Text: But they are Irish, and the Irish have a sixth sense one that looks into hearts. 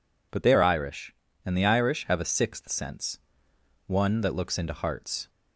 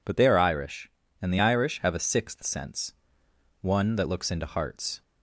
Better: neither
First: pauses between "sense" and "one"; noticeable; at 3.1 s; 0.68 s long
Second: pauses between "sense" and "one"; noticeable; at 2.9 s; 0.68 s long

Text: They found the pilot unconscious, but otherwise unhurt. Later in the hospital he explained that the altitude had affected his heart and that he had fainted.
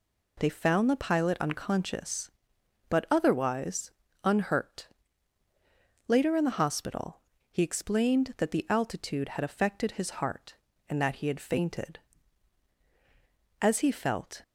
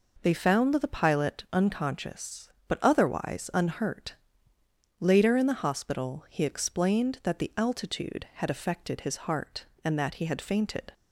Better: second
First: pauses between "otherwise" and "unhurt"; slight; at 3.9 s; 0.34 s long // pauses between "hospital" and "he"; slight; at 7.2 s; 0.30 s long // goes on to say "As he felt"; noticeable; from 13.6 s on; 0.82 s long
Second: none

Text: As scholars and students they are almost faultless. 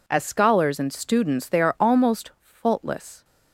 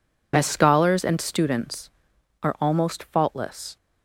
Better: first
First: none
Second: skips "they"; at 2.1 s

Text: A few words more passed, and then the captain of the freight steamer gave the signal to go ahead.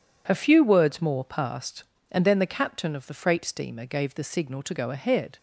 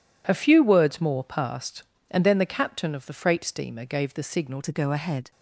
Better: first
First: none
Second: changes voice at "to"; from 4.6 s on; 0.7 s long

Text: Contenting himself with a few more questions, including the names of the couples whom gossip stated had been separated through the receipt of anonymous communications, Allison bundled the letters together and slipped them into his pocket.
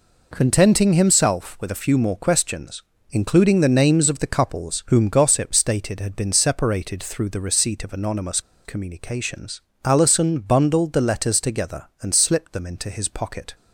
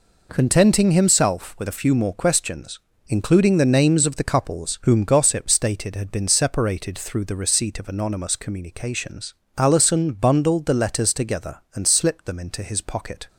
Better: second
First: pauses between "anonymous" and "communications"; slight; at 8.4 s; 0.24 s long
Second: none

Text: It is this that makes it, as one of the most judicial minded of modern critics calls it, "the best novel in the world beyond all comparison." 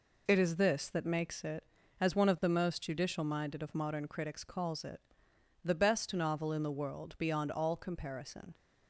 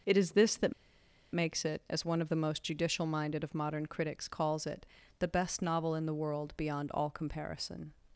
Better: first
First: none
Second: pauses between "that" and "makes"; noticeable; at 0.7 s; 0.59 s long

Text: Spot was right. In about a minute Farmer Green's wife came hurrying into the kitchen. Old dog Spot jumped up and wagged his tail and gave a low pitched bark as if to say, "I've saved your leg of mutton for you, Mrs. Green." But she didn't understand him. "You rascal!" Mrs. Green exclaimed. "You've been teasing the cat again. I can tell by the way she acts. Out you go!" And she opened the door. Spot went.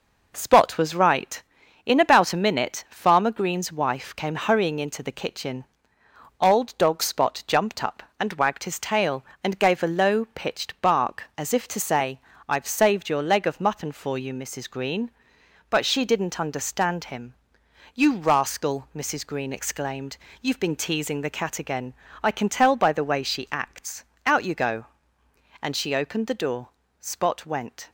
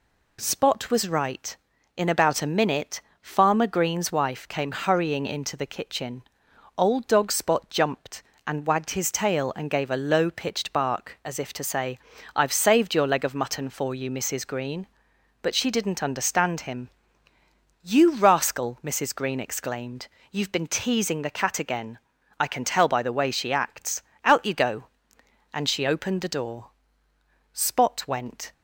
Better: first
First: none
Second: pauses between "minute" and "Farmer"; slight; at 3.0 s; 0.18 s long // skips "up"; at 8.3 s

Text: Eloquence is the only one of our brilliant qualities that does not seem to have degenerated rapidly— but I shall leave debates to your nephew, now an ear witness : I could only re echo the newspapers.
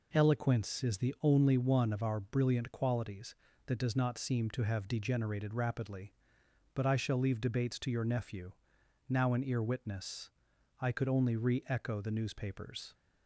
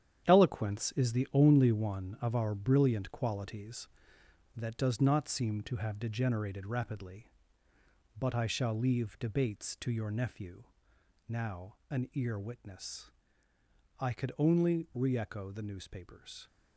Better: first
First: none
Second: gets quieter; strong; throughout; 8 dB // pauses between "now" and "an"; slight; at 11.7 s; 0.16 s long

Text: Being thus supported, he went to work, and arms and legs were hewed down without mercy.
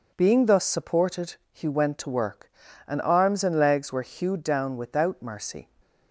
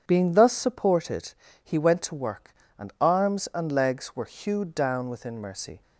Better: first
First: none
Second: starts louder than the rest; strong; until 1.0 s; 8.5 dB // says "within" for "without"; at 5.0 s

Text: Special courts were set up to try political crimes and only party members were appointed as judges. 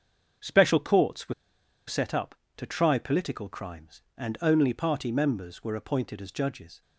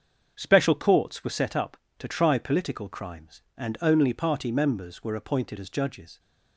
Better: second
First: starts louder than the rest; until 1.9 s; 7 dB // pauses between "were" and "set"; noticeable; at 1.3 s; 0.53 s long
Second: starts louder than the rest; until 1.3 s; 7 dB

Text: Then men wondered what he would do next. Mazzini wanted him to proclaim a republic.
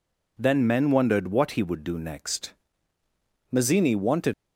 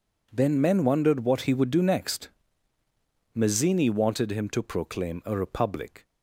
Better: second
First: stops before "him to proclaim a republic"; at 4.3 s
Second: none

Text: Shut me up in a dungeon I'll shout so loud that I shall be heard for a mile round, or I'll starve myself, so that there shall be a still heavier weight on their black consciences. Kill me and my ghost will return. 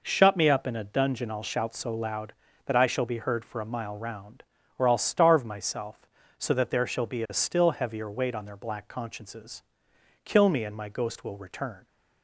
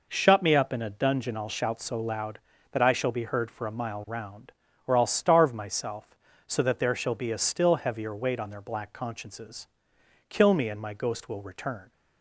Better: neither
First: none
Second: none

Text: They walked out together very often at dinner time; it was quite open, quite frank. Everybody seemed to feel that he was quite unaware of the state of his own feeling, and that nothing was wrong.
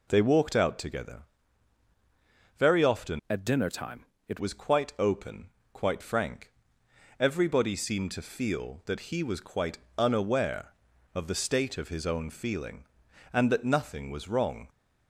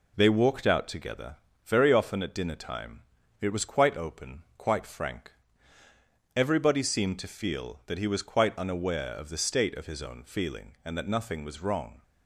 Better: second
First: pauses between "together" and "very"; strong; at 1.2 s; 1.3 s long // changes voice from "at" to "it"; from 3.2 to 4.3 s; 1.1 s long // pauses between "quite" and "unaware"; slight; at 9.7 s; 0.20 s long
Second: pauses between "together" and "very"; slight; at 1.3 s; 0.30 s long

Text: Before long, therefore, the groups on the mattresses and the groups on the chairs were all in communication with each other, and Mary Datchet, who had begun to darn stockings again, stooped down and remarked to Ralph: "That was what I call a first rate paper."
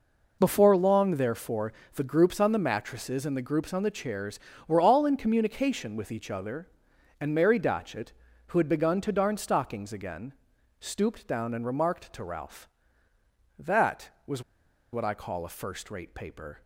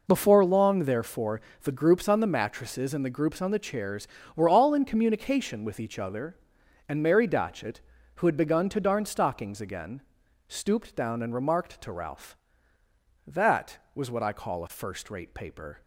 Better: second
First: pauses between "was" and "what"; noticeable; at 14.4 s; 0.52 s long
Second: none

